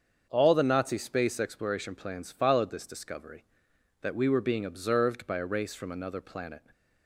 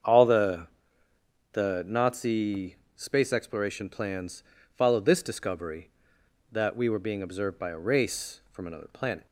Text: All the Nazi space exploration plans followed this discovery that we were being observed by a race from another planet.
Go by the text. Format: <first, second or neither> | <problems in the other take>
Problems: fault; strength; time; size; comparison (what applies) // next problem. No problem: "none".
first | starts louder than the rest; strong; until 1.9 s; 7.5 dB; also in the first // says "the" twice; at 1.5 s // pauses between "Nazi" and "space"; slight; at 2.7 s; 0.20 s long // pauses between "plans" and "followed"; slight; at 4.4 s; 0.32 s long